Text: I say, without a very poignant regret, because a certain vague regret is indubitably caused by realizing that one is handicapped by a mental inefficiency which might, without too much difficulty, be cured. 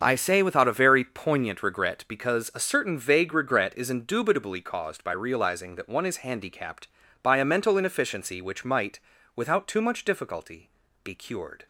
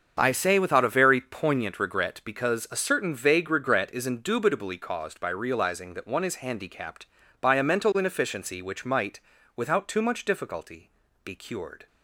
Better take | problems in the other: neither | starts louder than the rest; the same in both

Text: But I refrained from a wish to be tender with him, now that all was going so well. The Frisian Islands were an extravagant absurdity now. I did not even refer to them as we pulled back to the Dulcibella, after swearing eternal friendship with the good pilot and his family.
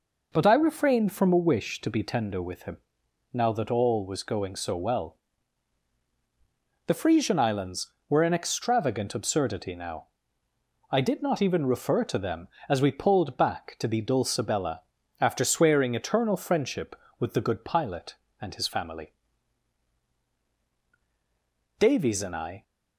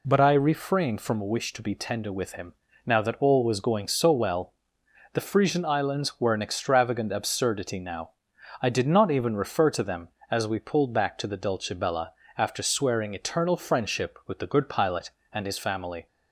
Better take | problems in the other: second | goes on to say "Davies and I"; noticeable; from 21.7 s on; 0.84 s long

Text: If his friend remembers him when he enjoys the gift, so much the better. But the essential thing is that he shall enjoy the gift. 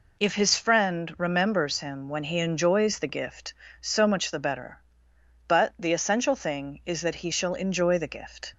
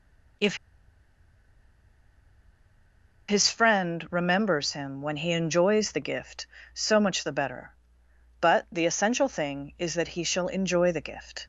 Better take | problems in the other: first | pauses between "If" and "his"; strong; at 0.5 s; 2.7 s long

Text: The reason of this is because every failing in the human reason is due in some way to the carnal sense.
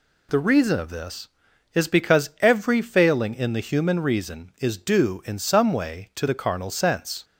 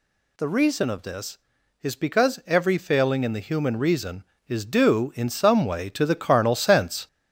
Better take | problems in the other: first | gets louder; noticeable; throughout; 4.5 dB

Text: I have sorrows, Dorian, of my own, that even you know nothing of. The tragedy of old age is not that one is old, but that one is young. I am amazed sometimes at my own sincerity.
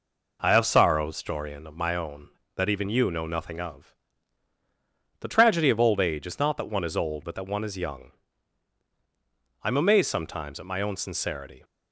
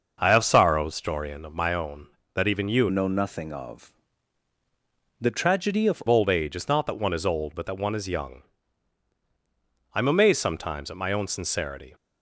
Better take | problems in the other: first | starts louder than the rest; until 1.2 s; 6 dB // changes voice from "know" to "of"; from 2.9 to 6.0 s; 3.1 s long

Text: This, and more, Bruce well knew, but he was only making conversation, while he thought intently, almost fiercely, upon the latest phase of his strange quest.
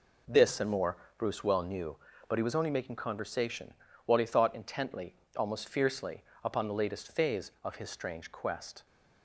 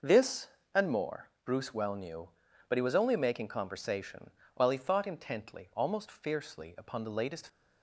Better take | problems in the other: first | stops before "phase of his strange quest"; at 7.4 s

